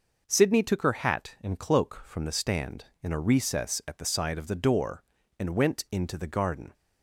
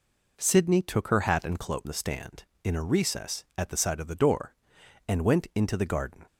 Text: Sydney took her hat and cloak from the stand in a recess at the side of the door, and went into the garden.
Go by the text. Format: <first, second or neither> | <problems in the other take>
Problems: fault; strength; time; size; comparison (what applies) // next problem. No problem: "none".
first | skips "from"; at 1.8 s